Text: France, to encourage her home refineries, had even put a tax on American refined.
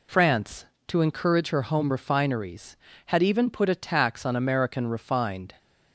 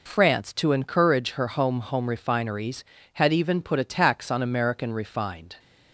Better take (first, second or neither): first